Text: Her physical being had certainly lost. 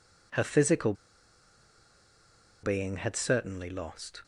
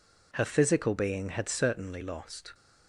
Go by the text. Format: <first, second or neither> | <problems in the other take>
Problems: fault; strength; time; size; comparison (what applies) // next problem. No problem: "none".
second | pauses between "physical" and "being"; strong; at 0.9 s; 1.7 s long